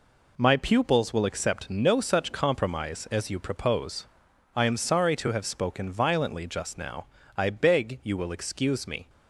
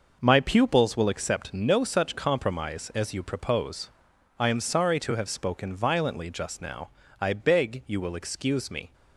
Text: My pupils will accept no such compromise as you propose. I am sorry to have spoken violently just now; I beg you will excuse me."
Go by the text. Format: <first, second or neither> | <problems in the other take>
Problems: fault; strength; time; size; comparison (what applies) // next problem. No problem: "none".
first | starts louder than the rest; noticeable; until 1.2 s; 6 dB